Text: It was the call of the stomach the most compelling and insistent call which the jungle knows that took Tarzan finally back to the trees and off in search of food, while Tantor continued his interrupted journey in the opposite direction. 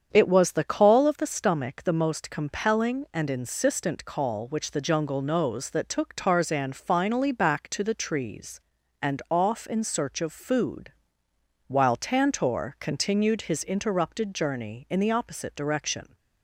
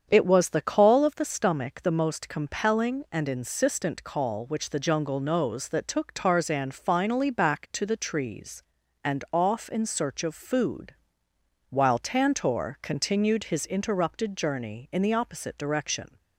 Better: neither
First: starts louder than the rest; strong; until 1.1 s; 7.5 dB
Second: starts louder than the rest; strong; until 1.1 s; 7.5 dB

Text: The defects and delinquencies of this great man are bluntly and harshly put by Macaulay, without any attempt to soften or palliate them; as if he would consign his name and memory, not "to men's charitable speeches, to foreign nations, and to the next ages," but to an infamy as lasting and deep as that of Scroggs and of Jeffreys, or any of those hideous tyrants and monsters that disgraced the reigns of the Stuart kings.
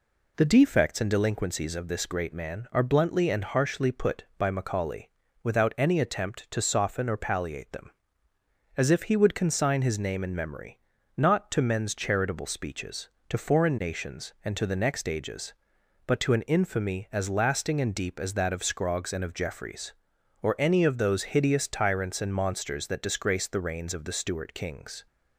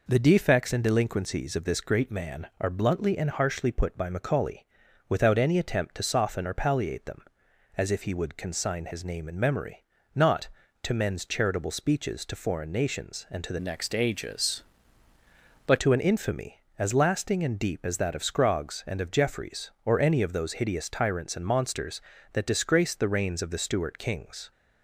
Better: first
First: none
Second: changes voice from "next" to "but"; from 13.5 to 15.7 s; 2.2 s long

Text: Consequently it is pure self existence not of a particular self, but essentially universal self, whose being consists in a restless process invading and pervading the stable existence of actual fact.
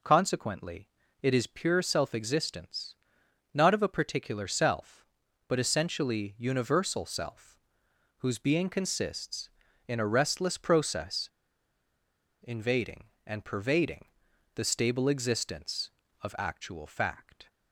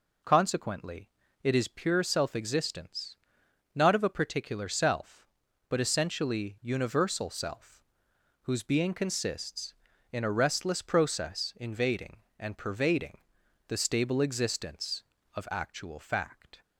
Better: second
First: pauses between "Consequently" and "it"; slight; at 0.8 s; 0.34 s long // pauses between "existence" and "not"; noticeable; at 2.9 s; 0.58 s long // pauses between "process" and "invading"; at 11.2 s; 1.1 s long // pauses between "pervading" and "the"; noticeable; at 14.0 s; 0.50 s long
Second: pauses between "Consequently" and "it"; slight; at 1.0 s; 0.34 s long // pauses between "existence" and "not"; noticeable; at 3.1 s; 0.58 s long // pauses between "pervading" and "the"; noticeable; at 13.1 s; 0.50 s long

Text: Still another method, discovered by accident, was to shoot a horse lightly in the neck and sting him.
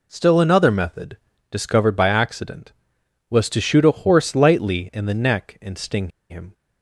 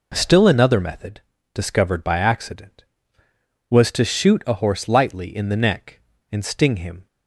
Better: second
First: pauses between "sting" and "him"; slight; at 6.0 s; 0.20 s long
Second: none

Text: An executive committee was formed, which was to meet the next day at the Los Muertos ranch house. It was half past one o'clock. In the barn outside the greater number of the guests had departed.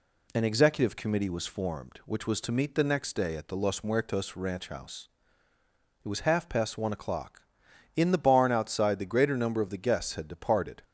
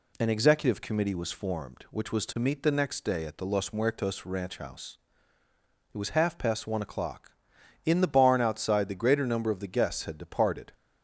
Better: neither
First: none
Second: none

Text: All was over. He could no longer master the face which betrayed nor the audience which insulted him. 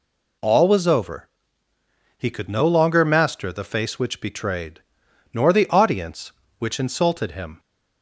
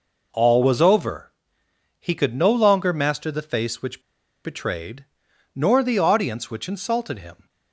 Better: first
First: pauses between "betrayed" and "nor"; noticeable; at 4.7 s; 0.54 s long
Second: pauses between "which" and "betrayed"; at 4.0 s; 0.44 s long // pauses between "betrayed" and "nor"; noticeable; at 5.0 s; 0.50 s long

